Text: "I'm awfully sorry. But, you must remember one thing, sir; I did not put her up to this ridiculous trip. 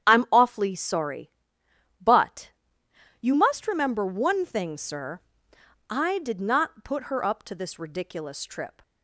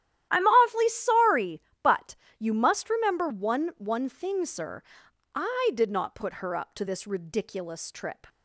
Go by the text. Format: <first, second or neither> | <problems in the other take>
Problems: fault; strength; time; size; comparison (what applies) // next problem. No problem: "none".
first | starts louder than the rest; strong; until 1.3 s; 12 dB; strong in the first // says "one" twice; at 3.7 s